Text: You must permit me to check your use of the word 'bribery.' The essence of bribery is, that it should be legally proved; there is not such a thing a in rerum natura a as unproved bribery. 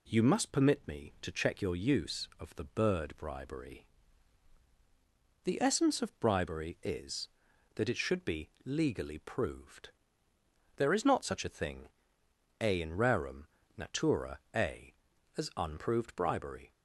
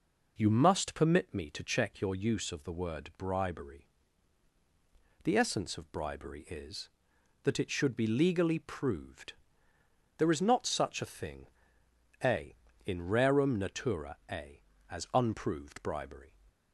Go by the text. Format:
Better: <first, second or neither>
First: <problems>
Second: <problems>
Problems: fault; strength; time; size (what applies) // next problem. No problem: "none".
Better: second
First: says "bird" for "word"; at 2.6 s // pauses between "thing" and "a"; noticeable; at 11.8 s; 0.74 s long // pauses between "rerum" and "natura"; slight; at 13.4 s; 0.30 s long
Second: pauses between "thing" and "a"; noticeable; at 11.4 s; 0.76 s long